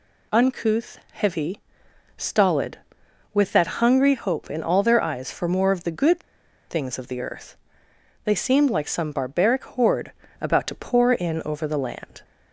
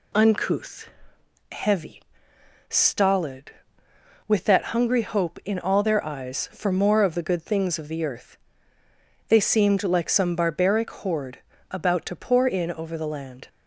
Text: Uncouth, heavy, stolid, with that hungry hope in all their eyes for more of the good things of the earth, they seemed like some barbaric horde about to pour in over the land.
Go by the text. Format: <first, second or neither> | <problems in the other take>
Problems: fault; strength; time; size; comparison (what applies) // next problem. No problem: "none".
second | pauses between "good" and "things"; noticeable; at 6.2 s; 0.47 s long // pauses between "horde" and "about"; slight; at 10.1 s; 0.30 s long; slight in the second